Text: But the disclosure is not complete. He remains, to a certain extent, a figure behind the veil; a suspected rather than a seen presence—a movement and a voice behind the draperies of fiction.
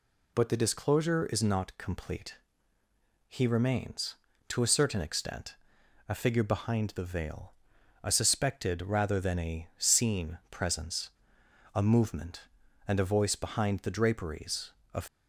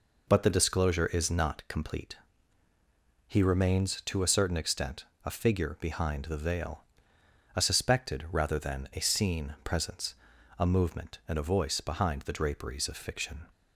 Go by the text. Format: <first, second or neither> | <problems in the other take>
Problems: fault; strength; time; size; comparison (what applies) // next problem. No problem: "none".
second | stops before "fiction"; at 15.0 s